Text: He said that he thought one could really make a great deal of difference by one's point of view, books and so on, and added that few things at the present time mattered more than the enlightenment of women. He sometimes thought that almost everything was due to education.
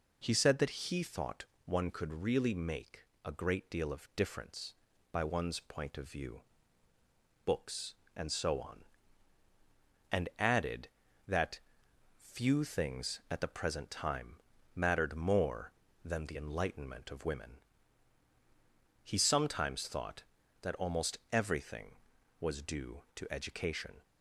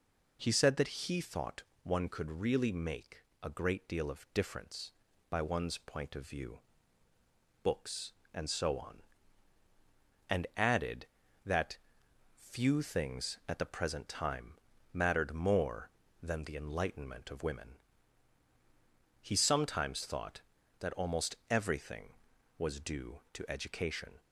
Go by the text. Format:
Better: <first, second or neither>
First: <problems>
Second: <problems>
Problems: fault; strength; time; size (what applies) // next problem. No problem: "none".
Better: neither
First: pauses between "thought" and "one"; slight; at 1.4 s; 0.18 s long // pauses between "make" and "a"; slight; at 3.0 s; 0.24 s long // pauses between "that" and "few"; noticeable; at 11.5 s; 0.58 s long // pauses between "time" and "mattered"; at 14.3 s; 0.40 s long // pauses between "almost" and "everything"; slight; at 21.1 s; 0.16 s long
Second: pauses between "thought" and "one"; slight; at 1.6 s; 0.18 s long // pauses between "make" and "a"; slight; at 3.1 s; 0.24 s long // pauses between "that" and "few"; noticeable; at 11.7 s; 0.58 s long // pauses between "time" and "mattered"; at 14.5 s; 0.40 s long // pauses between "almost" and "everything"; slight; at 21.3 s; 0.16 s long